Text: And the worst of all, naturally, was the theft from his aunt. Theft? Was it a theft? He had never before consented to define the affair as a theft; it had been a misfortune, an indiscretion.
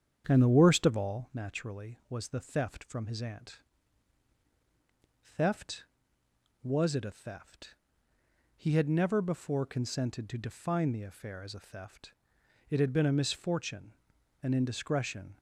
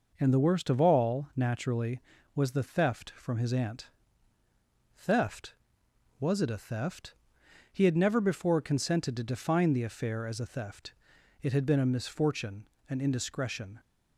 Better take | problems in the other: second | starts louder than the rest; strong; until 1.4 s; 8.5 dB

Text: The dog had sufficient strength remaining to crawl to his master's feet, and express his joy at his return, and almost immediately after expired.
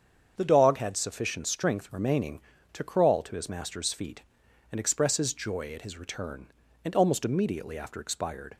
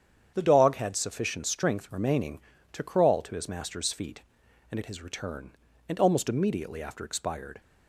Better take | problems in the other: first | starts louder than the rest; strong; until 1.3 s; 8.5 dB; strong in the first // skips "express his joy"; at 4.7 s

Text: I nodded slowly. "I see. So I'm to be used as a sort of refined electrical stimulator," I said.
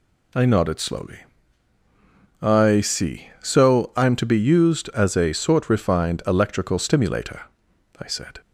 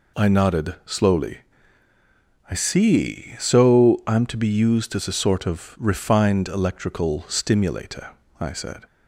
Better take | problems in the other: second | skips "of"; at 5.7 s

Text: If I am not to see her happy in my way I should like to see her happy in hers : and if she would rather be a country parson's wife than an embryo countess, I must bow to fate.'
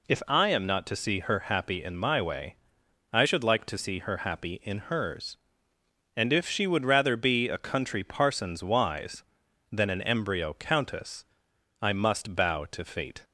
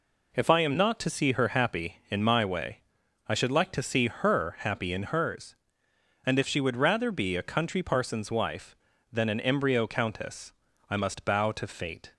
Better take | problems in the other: second | pauses between "way" and "I"; noticeable; at 2.5 s; 0.56 s long; noticeable in the second // says "wise" for "wife"; at 8.6 s

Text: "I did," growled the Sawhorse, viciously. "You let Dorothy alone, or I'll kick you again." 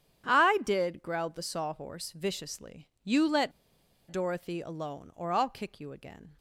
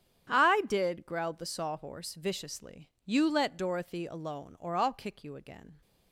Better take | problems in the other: second | starts louder than the rest; strong; until 1.3 s; 9.5 dB; strong in the second // pauses between "let" and "Dorothy"; noticeable; at 3.5 s; 0.59 s long

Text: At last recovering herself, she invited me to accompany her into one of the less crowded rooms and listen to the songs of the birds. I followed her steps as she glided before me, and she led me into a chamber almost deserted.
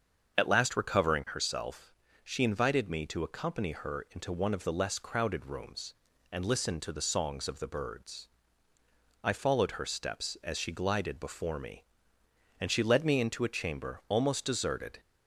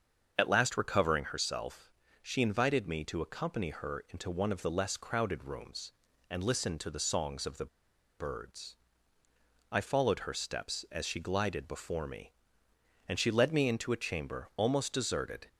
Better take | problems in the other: first | starts louder than the rest; until 1.3 s; 7 dB; also in the first // pauses between "the" and "birds"; noticeable; at 7.6 s; 0.52 s long

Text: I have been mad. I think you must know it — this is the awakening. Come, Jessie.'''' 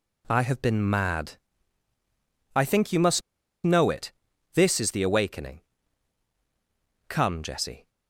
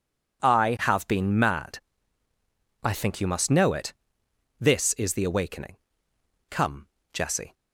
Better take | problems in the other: second | pauses between "must" and "know"; at 3.2 s; 0.43 s long

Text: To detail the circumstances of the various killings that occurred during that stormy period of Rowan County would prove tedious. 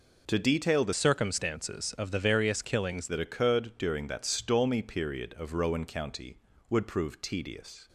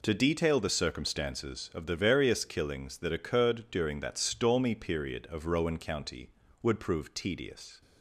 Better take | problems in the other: second | changes voice from "circumstances" to "killings"; from 0.9 to 3.0 s; 2.1 s long

